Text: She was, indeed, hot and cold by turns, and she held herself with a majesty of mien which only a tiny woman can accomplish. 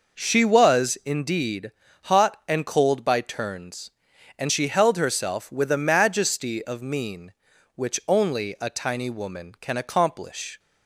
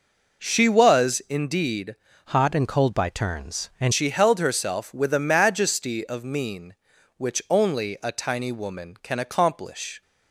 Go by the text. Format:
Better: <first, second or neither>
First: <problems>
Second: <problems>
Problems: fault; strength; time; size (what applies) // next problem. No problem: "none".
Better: first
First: none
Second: changes voice from "hot" to "and"; from 2.2 to 3.9 s; 1.7 s long